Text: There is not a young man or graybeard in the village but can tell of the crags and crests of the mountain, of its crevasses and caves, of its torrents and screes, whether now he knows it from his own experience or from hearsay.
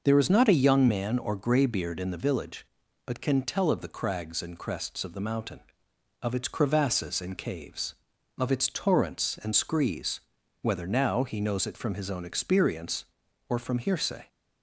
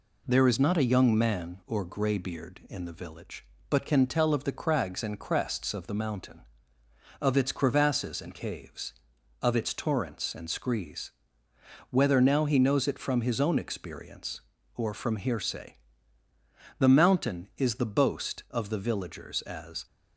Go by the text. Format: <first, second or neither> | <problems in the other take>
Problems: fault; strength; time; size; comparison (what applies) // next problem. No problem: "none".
first | goes on to say "The mountain is the boast of the villagers as"; strong; from 16.7 s on; 3.0 s long